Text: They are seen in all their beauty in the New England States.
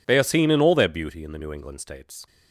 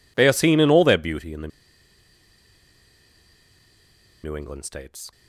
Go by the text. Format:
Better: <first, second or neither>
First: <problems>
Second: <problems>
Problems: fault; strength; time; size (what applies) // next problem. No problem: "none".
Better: first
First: none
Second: pauses between "the" and "New"; strong; at 1.4 s; 2.7 s long